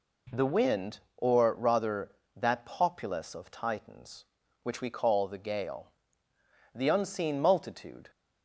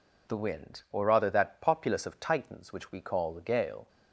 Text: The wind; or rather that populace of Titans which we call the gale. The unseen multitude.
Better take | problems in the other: first | stops before "The unseen multitude"; at 3.8 s

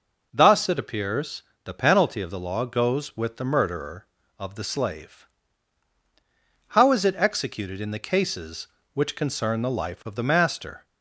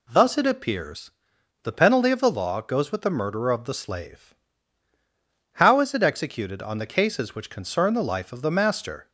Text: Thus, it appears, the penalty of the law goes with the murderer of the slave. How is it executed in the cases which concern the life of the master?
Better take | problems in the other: first | says "on" for "in"; at 6.6 s

